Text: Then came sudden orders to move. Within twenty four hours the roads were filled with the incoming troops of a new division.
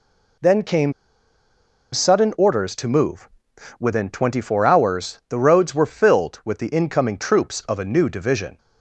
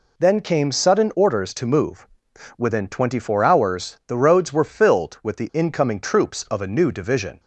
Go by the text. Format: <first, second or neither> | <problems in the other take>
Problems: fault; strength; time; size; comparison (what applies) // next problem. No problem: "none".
second | pauses between "came" and "sudden"; at 0.9 s; 1.0 s long